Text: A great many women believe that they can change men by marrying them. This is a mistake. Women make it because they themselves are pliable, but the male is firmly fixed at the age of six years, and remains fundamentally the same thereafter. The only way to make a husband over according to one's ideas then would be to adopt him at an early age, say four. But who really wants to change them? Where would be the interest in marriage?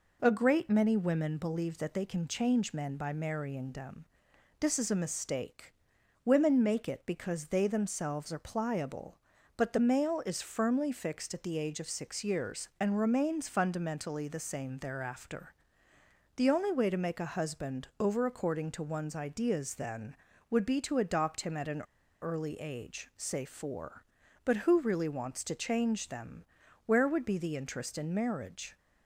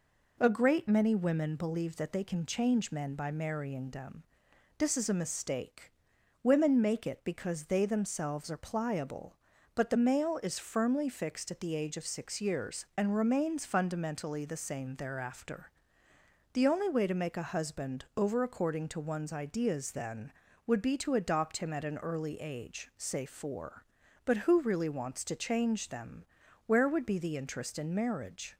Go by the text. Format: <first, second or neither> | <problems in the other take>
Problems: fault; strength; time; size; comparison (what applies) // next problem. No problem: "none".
second | pauses between "an" and "early"; at 21.8 s; 0.40 s long